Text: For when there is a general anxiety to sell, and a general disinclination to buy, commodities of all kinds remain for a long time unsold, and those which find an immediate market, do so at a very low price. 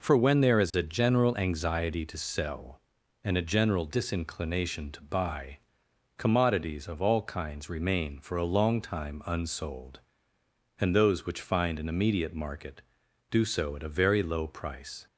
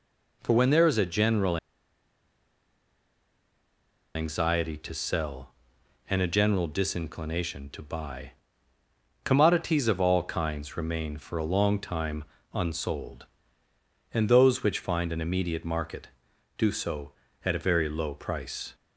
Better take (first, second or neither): first